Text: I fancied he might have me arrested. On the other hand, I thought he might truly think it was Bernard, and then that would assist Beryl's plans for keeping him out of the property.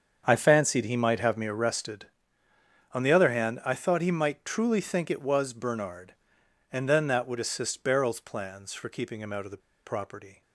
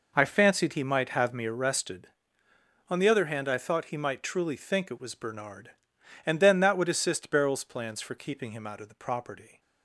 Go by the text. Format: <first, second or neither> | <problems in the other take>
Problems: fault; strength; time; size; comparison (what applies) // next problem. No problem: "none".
second | starts louder than the rest; strong; until 1.2 s; 7 dB // pauses between "the" and "property"; slight; at 9.5 s; 0.27 s long